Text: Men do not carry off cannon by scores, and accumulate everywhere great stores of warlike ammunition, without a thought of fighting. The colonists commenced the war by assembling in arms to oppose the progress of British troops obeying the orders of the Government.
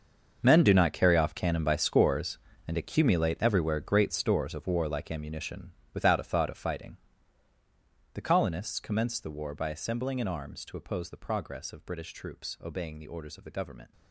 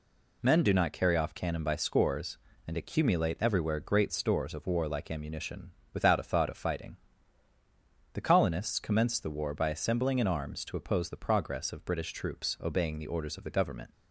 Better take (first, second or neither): second